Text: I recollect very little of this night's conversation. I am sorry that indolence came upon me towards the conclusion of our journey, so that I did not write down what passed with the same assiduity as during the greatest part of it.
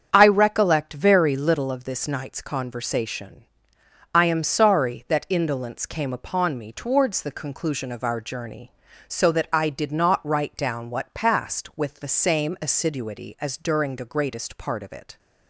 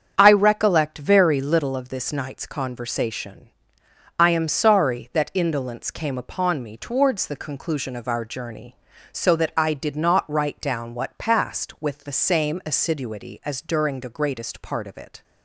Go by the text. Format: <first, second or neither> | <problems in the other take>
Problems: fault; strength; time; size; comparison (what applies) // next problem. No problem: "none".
neither | starts louder than the rest; strong; the same in both